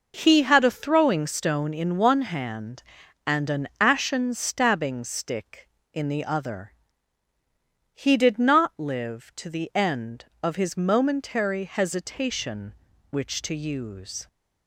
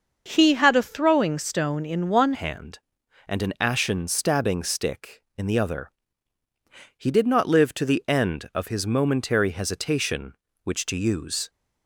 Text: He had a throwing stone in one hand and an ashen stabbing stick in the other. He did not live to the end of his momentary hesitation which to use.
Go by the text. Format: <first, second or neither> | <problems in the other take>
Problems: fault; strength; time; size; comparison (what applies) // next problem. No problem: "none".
first | starts louder than the rest; until 1.2 s; 6.5 dB // changes voice at "hand"; from 2.3 s on; 9.1 s long